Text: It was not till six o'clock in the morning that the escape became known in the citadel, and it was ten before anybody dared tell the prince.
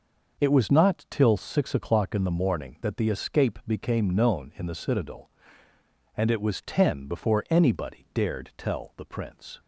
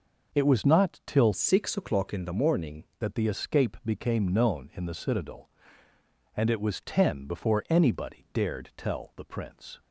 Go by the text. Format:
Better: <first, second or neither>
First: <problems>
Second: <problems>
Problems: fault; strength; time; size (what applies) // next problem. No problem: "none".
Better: first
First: none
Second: changes voice from "six" to "morning"; from 1.3 to 2.8 s; 1.5 s long